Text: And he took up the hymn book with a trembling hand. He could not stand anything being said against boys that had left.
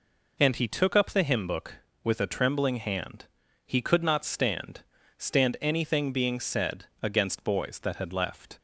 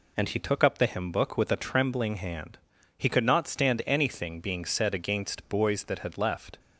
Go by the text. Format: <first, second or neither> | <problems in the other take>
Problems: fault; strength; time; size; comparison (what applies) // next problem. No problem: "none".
second | says "stand" twice; at 5.1 s